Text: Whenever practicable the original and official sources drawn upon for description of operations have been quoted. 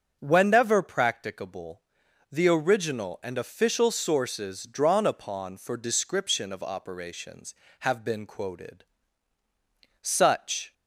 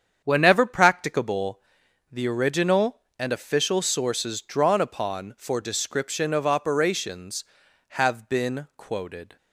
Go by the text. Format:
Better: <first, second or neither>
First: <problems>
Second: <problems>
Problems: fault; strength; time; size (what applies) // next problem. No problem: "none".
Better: second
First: starts louder than the rest; strong; until 1.2 s; 7.5 dB // pauses between "practicable" and "the"; noticeable; at 1.7 s; 0.50 s long // goes on to say "Such"; noticeable; from 10.0 s on; 0.72 s long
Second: starts louder than the rest; strong; until 1.2 s; 8 dB // pauses between "practicable" and "the"; noticeable; at 1.5 s; 0.52 s long